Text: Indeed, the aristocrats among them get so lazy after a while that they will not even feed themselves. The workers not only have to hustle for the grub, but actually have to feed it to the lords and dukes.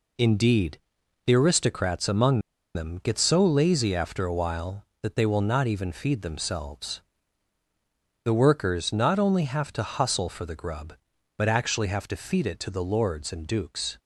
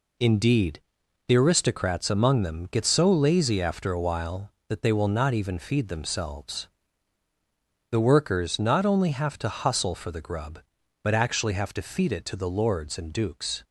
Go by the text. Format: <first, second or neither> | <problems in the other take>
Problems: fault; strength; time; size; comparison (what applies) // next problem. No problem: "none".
second | pauses between "among" and "them"; slight; at 2.4 s; 0.34 s long